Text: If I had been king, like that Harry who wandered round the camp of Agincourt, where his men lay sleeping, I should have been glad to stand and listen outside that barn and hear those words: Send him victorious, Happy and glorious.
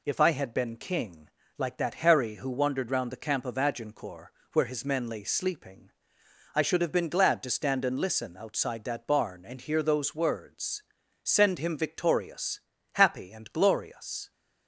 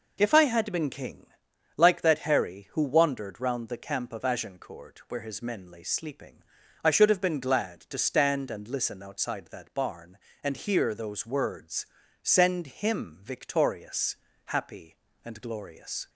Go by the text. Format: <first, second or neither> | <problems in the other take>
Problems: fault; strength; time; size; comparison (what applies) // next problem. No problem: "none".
neither | none